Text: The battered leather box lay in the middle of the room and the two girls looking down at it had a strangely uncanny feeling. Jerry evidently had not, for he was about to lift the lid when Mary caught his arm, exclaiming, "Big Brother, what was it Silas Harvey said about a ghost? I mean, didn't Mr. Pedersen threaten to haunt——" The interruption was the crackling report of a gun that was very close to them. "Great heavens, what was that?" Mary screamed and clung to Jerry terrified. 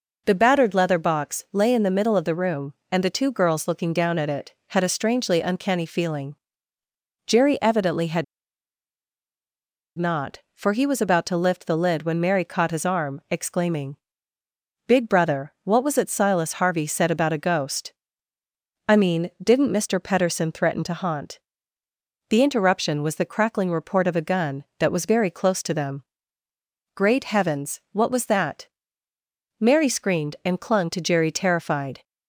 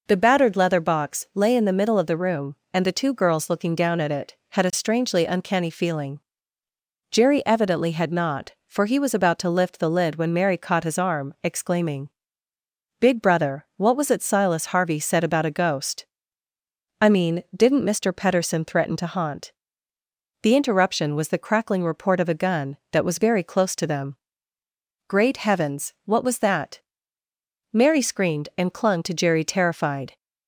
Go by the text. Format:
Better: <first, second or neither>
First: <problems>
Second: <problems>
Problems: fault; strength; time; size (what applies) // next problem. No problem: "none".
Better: second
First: pauses between "had" and "not"; strong; at 8.2 s; 1.7 s long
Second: none